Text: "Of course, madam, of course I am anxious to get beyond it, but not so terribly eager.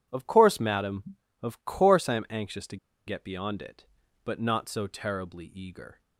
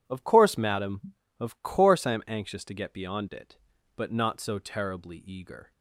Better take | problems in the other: second | pauses between "to" and "get"; slight; at 2.7 s; 0.31 s long

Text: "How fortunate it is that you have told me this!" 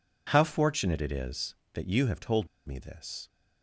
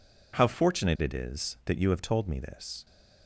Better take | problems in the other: second | pauses between "told" and "me"; slight; at 2.4 s; 0.20 s long

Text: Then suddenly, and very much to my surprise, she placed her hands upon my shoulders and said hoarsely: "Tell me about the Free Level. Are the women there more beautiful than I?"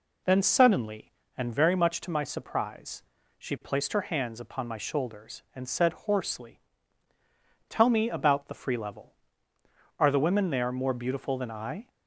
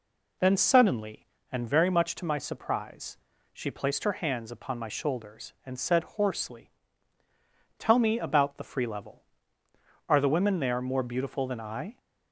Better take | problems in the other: neither | none

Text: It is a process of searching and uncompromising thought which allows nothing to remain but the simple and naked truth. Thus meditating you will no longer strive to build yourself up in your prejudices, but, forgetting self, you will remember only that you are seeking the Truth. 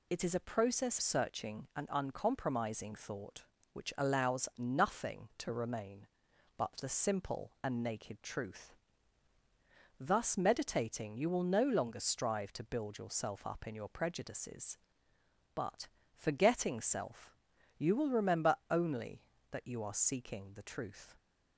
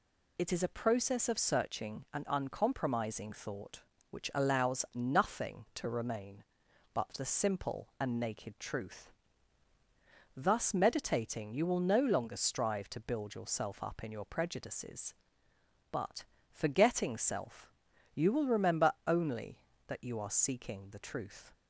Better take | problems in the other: second | skips "of"; at 0.9 s

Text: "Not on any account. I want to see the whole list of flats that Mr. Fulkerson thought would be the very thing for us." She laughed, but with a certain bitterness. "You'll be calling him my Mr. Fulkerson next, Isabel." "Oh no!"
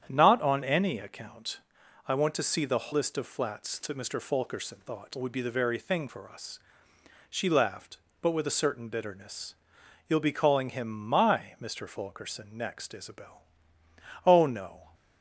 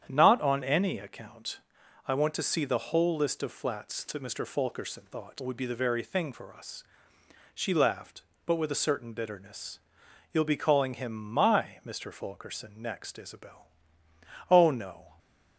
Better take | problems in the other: second | starts louder than the rest; strong; until 1.1 s; 9 dB; strong in the second // skips "whole"; at 2.9 s

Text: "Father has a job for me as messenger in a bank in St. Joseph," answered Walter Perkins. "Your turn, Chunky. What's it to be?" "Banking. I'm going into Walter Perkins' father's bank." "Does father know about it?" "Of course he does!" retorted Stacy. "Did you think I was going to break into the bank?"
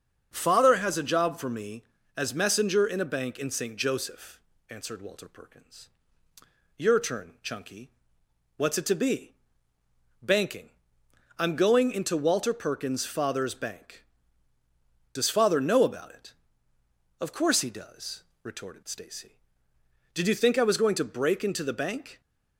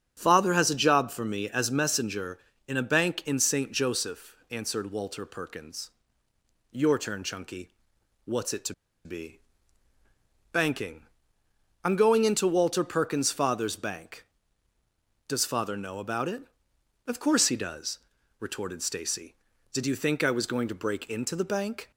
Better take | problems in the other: first | starts louder than the rest; strong; until 1.1 s; 8 dB; also in the first // pauses between "to" and "be"; slight; at 8.7 s; 0.31 s long

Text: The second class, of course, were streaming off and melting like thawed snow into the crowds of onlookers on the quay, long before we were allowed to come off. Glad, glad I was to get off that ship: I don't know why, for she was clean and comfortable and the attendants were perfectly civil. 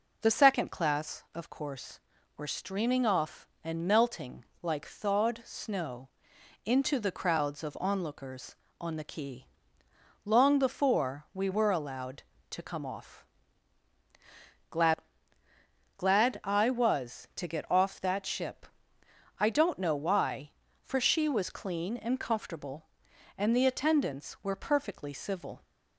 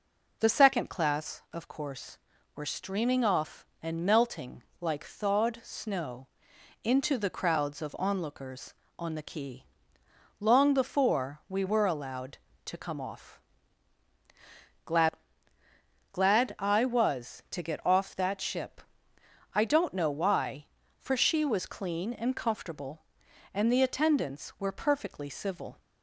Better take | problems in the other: neither | pauses between "melting" and "like"; slight; the same in both // pauses between "snow" and "into"; noticeable; the same in both

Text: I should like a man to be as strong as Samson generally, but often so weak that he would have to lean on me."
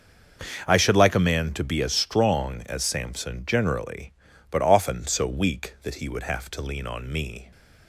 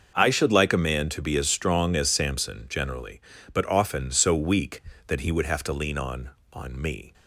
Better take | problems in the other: first | starts louder than the rest; until 1.1 s; 6 dB; also in the first // says "on" twice; at 6.5 s

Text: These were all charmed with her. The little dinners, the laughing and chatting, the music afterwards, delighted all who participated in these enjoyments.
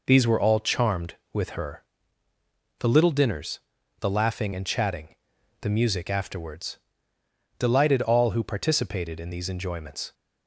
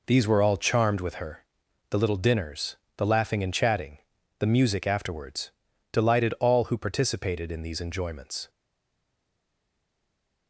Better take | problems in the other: first | stays silent after the last word; noticeable; from 8.4 s on; 2.0 s long

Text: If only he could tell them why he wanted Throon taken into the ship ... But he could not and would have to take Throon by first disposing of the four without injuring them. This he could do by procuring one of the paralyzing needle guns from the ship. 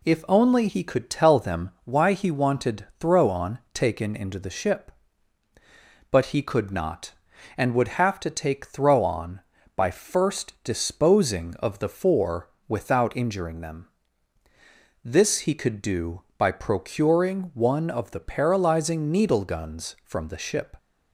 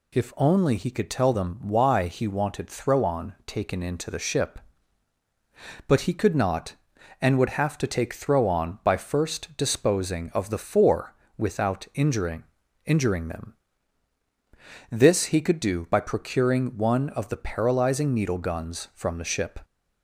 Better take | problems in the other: first | pauses between "four" and "without"; slight; at 11.1 s; 0.22 s long; slight in the first // says "injuring" twice; at 12.8 s

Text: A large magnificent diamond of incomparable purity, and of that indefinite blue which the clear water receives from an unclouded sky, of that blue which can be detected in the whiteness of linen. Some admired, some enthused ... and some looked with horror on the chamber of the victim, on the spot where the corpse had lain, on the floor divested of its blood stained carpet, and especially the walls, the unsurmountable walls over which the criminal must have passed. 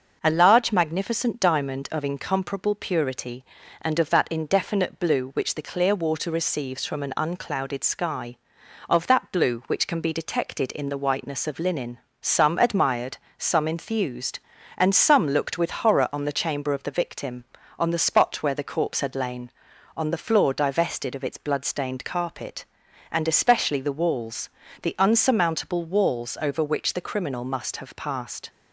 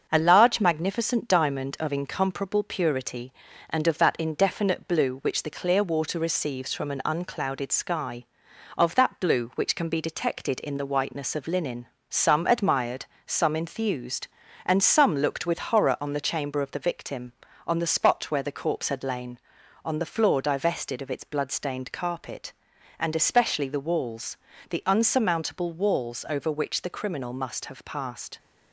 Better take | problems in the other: first | gets quieter; slight; throughout; 3 dB // starts louder than the rest; until 1.1 s; 6.5 dB; noticeable in the first

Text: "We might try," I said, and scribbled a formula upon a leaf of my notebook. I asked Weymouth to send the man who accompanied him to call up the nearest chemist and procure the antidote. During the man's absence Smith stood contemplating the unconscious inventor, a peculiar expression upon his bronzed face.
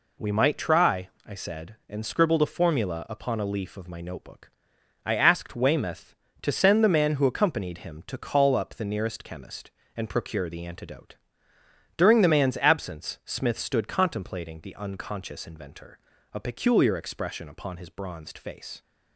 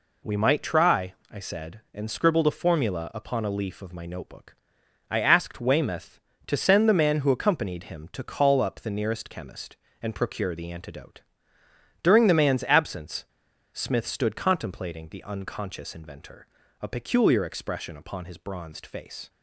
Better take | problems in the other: first | pauses between "absence" and "Smith"; noticeable; at 13.2 s; 0.47 s long

